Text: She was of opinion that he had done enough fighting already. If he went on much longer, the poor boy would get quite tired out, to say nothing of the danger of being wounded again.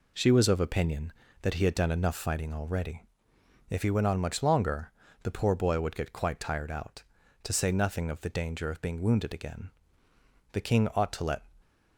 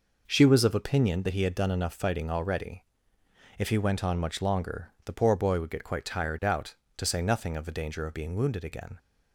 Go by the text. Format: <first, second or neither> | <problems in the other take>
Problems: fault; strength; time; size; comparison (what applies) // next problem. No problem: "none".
second | goes on to say "The King ought to let"; noticeable; from 10.5 s on; 0.92 s long